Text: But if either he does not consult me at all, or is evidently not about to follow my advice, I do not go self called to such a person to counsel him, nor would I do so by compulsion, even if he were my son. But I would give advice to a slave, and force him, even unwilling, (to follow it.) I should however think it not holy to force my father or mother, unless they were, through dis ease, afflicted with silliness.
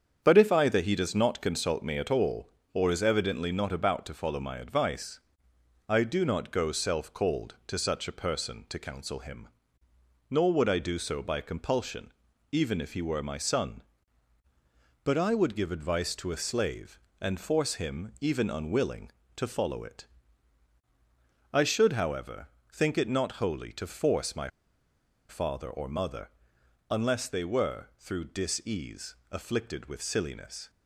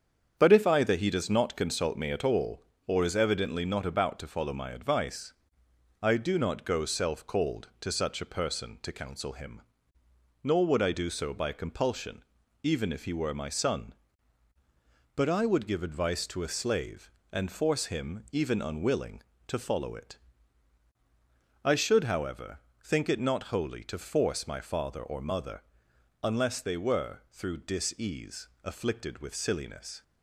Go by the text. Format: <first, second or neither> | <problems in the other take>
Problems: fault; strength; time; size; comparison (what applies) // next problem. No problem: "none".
second | starts louder than the rest; strong; until 1.2 s; 7.5 dB; strong in the second // pauses between "however" and "think"; slight; at 22.4 s; 0.24 s long; slight in the second // pauses between "my" and "father"; noticeable; at 24.4 s; 0.81 s long